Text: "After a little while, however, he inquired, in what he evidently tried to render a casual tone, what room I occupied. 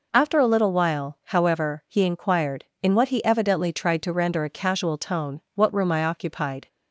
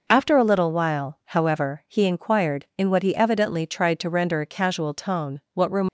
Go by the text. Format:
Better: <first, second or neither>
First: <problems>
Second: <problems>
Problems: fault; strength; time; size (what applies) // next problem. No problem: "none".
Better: first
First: none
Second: stops before "I occupied"; at 5.8 s